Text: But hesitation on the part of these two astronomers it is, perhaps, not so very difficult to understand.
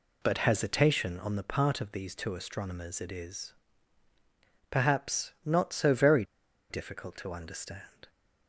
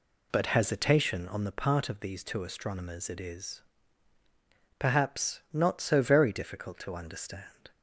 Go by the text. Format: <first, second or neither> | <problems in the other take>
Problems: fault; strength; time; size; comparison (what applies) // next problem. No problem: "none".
second | pauses between "very" and "difficult"; noticeable; at 6.2 s; 0.47 s long